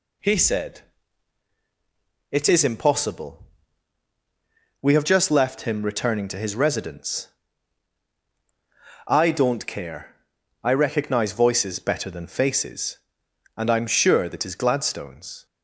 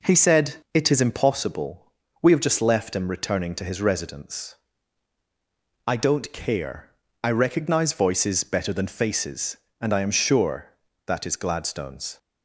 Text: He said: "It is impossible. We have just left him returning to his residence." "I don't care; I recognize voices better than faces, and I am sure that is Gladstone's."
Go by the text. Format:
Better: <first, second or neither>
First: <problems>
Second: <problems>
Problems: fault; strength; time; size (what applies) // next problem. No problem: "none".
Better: neither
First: none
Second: none